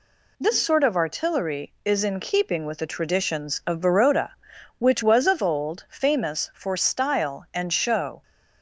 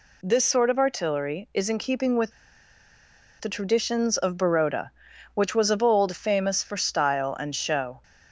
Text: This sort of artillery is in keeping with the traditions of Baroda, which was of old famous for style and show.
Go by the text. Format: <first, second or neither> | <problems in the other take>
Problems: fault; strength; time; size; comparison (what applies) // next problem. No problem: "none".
first | pauses between "with" and "the"; at 2.3 s; 1.0 s long